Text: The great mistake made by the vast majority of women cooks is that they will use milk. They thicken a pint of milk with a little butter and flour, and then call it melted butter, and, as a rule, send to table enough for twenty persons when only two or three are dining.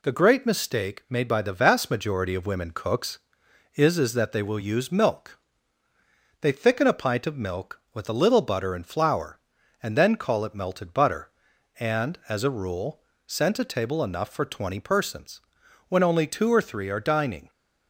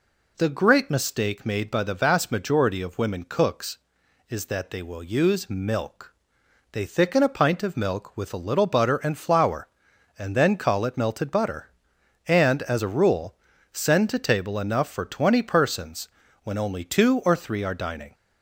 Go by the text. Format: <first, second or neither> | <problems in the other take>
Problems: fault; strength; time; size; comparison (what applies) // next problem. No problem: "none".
second | says "is" twice; at 3.9 s // pauses between "persons" and "when"; noticeable; at 15.3 s; 0.48 s long; slight in the second